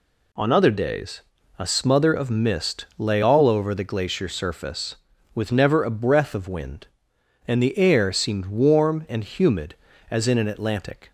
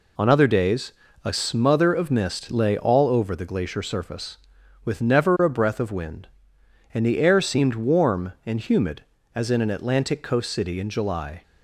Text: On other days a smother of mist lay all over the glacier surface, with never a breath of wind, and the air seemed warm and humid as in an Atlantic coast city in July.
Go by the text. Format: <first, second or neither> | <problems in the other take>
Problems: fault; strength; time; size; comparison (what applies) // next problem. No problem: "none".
second | pauses between "days" and "a"; at 1.1 s; 0.38 s long; slight in the second // stops before "coast city in July"; at 11.0 s